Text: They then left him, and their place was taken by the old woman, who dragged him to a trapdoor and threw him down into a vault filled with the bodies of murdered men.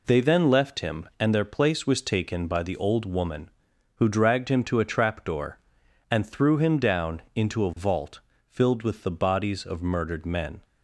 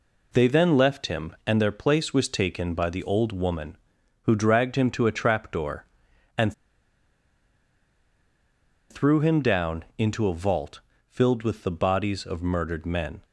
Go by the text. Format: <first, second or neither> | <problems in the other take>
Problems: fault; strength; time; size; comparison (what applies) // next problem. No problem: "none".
first | pauses between "and" and "threw"; strong; at 6.5 s; 2.3 s long // pauses between "vault" and "filled"; slight; at 10.8 s; 0.28 s long; slight in the first